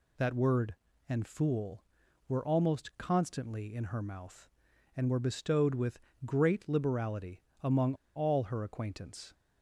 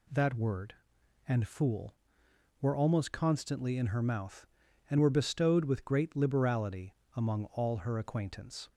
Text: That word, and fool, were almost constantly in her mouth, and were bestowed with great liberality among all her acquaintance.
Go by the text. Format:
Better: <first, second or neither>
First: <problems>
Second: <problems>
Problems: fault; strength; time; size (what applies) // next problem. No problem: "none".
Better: second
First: pauses between "with" and "great"; slight; at 6.0 s; 0.26 s long // pauses between "liberality" and "among"; slight; at 7.4 s; 0.20 s long // pauses between "among" and "all"; slight; at 7.9 s; 0.21 s long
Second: pauses between "liberality" and "among"; slight; at 6.9 s; 0.21 s long